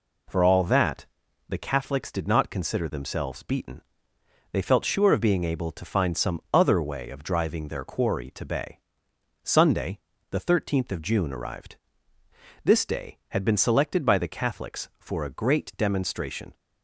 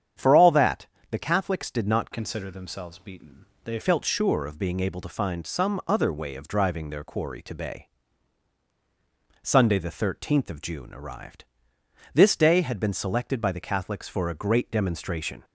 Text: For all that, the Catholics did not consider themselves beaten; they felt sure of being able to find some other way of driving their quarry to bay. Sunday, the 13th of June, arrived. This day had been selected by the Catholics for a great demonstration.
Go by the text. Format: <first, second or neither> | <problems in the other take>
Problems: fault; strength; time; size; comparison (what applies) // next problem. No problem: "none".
first | starts louder than the rest; strong; until 1.4 s; 8.5 dB // changes voice from "consider" to "they"; from 2.1 to 3.7 s; 1.6 s long